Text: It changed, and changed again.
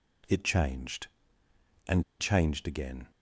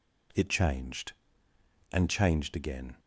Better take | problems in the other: second | pauses between "and" and "changed"; slight; at 2.0 s; 0.17 s long

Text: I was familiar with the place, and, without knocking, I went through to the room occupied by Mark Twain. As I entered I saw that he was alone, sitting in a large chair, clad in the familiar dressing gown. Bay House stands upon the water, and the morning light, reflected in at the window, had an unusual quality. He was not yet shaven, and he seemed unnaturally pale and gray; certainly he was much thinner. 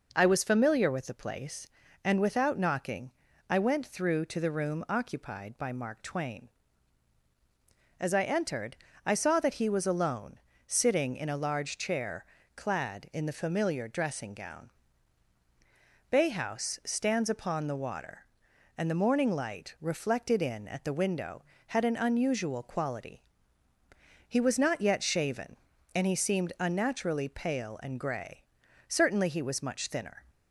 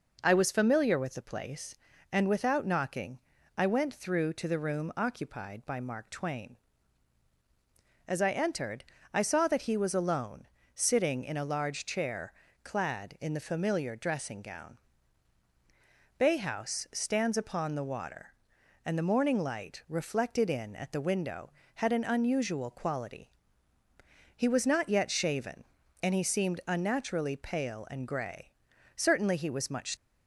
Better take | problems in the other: first | pauses between "entered" and "I"; slight; at 8.8 s; 0.30 s long; slight in the first // stops before "thinner"; at 29.9 s

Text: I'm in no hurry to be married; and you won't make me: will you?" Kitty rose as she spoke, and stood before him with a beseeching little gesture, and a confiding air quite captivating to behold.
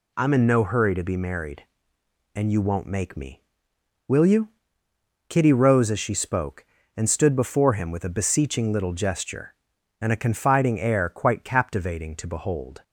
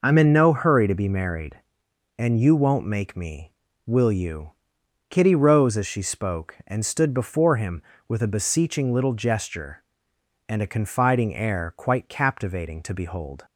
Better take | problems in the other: neither | none

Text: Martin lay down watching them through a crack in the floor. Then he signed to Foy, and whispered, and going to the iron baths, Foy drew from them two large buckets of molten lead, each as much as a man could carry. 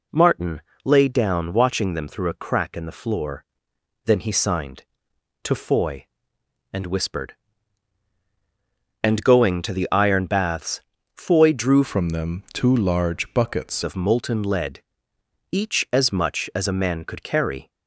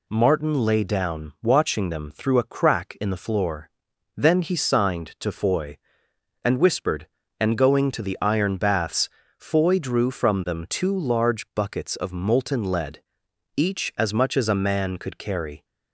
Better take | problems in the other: second | pauses between "Martin" and "lay"; slight; at 0.6 s; 0.22 s long // changes voice from "from" to "buckets"; from 11.8 to 13.8 s; 2.0 s long

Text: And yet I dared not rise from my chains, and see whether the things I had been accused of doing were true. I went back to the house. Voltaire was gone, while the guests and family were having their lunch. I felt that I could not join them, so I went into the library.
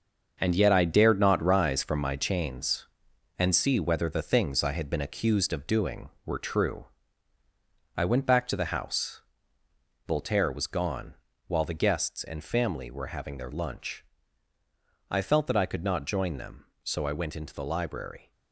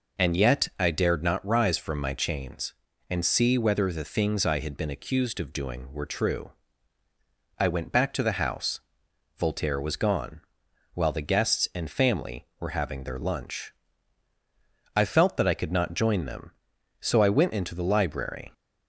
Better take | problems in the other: second | gets quieter; strong; throughout; 8 dB

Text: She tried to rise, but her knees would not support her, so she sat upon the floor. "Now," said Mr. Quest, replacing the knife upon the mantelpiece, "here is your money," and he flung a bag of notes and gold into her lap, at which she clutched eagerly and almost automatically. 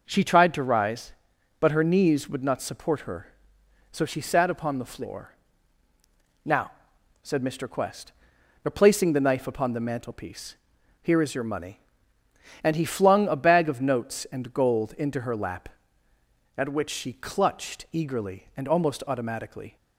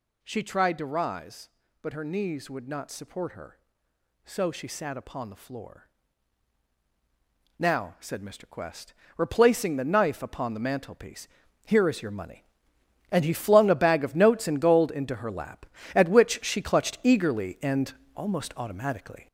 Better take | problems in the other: first | gets louder; throughout; 7 dB // pauses between "and" and "almost"; slight; at 17.9 s; 0.20 s long

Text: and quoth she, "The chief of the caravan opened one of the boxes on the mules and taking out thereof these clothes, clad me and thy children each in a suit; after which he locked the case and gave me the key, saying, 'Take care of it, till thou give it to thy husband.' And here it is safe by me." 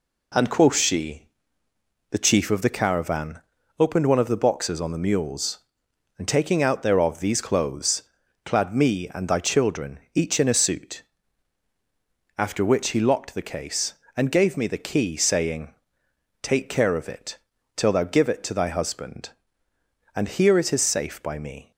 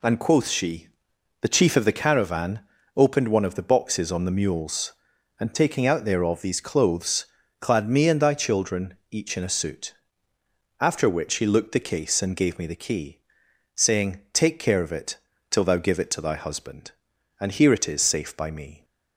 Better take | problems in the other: first | pauses between "caravan" and "opened"; slight; at 2.6 s; 0.36 s long; also in the first // pauses between "children" and "each"; slight; at 8.9 s; 0.16 s long; slight in the first // says "looked" for "locked"; at 11.4 s

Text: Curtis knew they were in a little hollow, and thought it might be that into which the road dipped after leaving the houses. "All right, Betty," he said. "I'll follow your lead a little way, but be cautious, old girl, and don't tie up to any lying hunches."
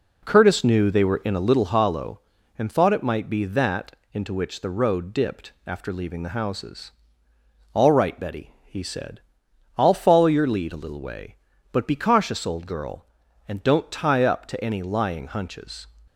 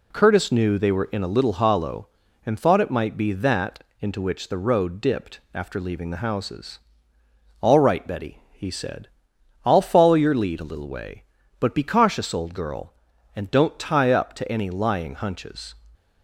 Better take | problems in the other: second | starts louder than the rest; until 1.8 s; 3.5 dB // pauses between "that" and "into"; slight; at 3.9 s; 0.18 s long; slight in the second

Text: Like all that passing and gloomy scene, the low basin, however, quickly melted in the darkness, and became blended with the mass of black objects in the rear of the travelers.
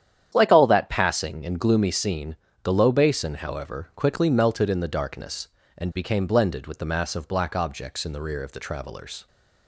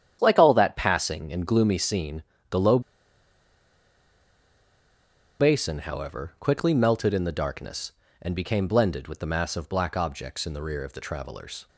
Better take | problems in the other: first | starts louder than the rest; strong; until 1.2 s; 9.5 dB; strong in the first // pauses between "low" and "basin"; strong; at 2.8 s; 2.5 s long

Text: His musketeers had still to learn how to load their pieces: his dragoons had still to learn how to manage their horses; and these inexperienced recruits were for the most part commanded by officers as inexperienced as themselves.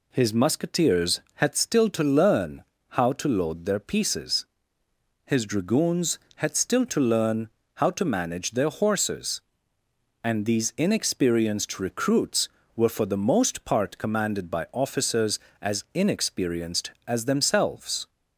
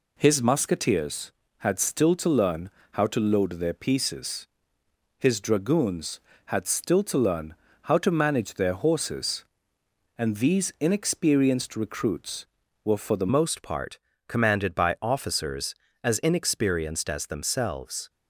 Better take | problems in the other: first | pauses between "learn" and "how"; slight; at 2.7 s; 0.22 s long; slight in the first // pauses between "learn" and "how"; slight; at 7.5 s; 0.28 s long; slight in the first // changes voice at "most"; from 13.3 s on; 4.7 s long // pauses between "part" and "commanded"; slight; at 13.9 s; 0.30 s long

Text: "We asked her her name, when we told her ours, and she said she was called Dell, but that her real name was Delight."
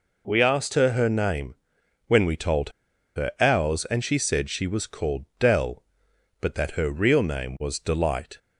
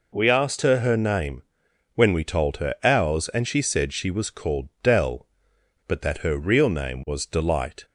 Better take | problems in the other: second | pauses between "told" and "her"; at 2.6 s; 0.45 s long // pauses between "called" and "Dell"; slight; at 5.2 s; 0.16 s long; slight in the second

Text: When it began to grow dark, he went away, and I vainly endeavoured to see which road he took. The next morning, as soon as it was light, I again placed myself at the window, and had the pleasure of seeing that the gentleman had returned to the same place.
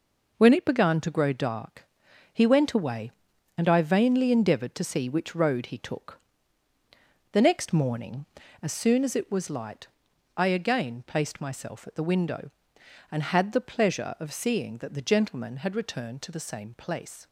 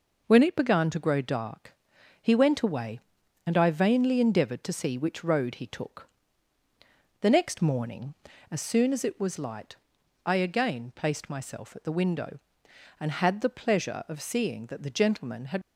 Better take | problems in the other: first | stops before "returned to the same place"; at 15.6 s

